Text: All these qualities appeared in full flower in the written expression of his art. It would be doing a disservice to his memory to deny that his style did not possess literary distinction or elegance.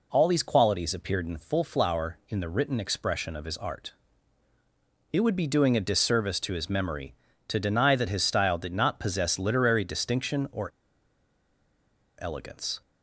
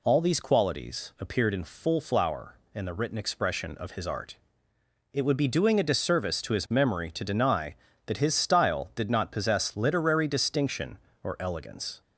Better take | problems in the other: second | pauses between "or" and "elegance"; strong; at 10.6 s; 1.5 s long

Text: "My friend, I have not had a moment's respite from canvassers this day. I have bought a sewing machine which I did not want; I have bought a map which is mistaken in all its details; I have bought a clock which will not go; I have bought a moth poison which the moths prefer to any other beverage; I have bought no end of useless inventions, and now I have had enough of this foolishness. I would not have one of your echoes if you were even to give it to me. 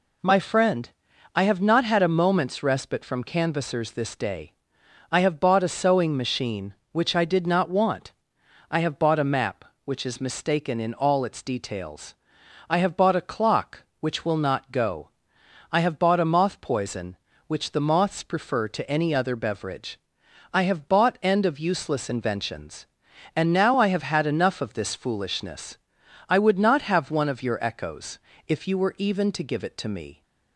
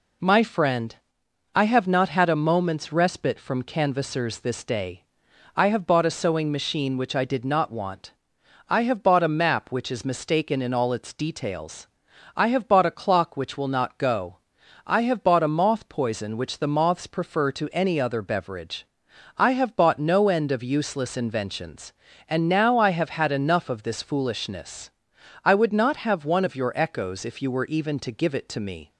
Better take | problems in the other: second | skips "no"; at 21.2 s // pauses between "echoes" and "if"; slight; at 28.1 s; 0.30 s long

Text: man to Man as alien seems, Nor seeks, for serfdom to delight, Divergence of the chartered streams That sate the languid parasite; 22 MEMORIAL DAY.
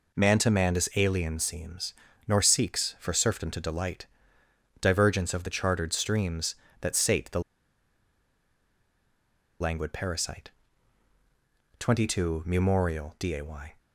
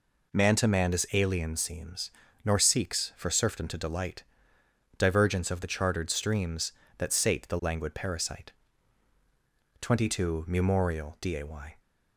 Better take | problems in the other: second | pauses between "the" and "languid"; strong; at 7.4 s; 2.1 s long

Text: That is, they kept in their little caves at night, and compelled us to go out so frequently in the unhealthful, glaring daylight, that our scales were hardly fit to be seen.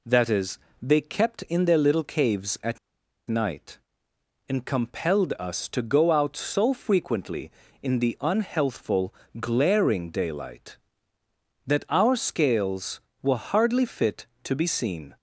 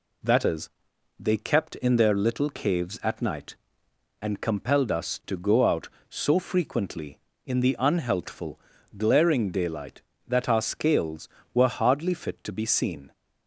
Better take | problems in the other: second | pauses between "at" and "night"; noticeable; at 2.7 s; 0.49 s long

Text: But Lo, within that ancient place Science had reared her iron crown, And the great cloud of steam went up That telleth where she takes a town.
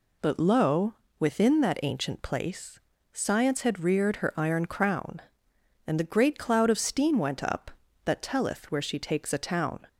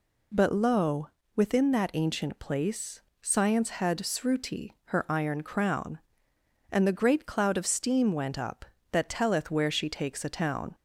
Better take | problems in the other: first | pauses between "place" and "Science"; slight; at 3.0 s; 0.24 s long; slight in the first // says "sruti" for "reared"; at 3.9 s

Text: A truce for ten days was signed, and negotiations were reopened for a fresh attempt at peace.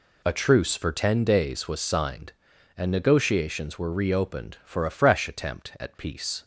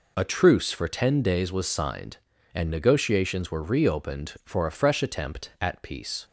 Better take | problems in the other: neither | none

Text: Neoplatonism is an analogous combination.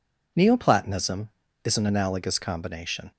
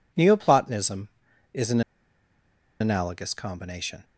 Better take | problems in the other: first | pauses between "an" and "analogous"; at 1.8 s; 0.99 s long

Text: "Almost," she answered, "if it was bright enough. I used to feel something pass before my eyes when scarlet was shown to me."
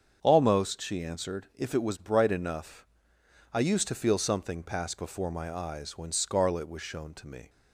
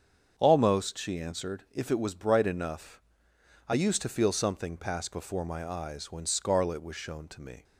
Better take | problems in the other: neither | starts louder than the rest; strong; the same in both

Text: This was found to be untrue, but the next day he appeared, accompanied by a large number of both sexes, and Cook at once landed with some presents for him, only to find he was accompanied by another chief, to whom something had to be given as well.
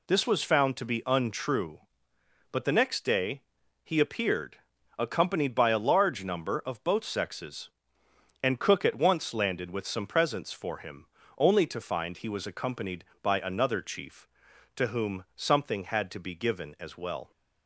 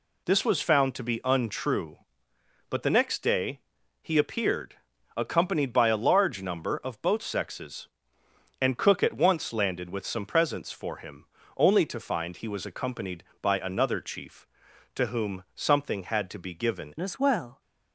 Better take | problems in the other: first | pauses between "day" and "he"; at 3.5 s; 0.40 s long; also in the first // changes voice at "as"; from 17.0 s on; 0.6 s long

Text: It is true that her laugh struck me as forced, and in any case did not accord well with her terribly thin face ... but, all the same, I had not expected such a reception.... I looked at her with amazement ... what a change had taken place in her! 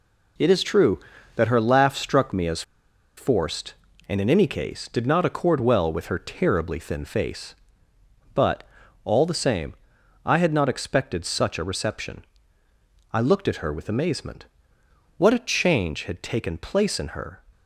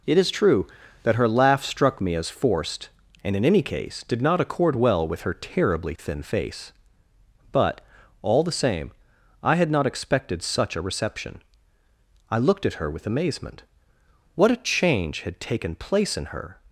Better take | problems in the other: second | pauses between "as" and "forced"; noticeable; at 2.6 s; 0.55 s long

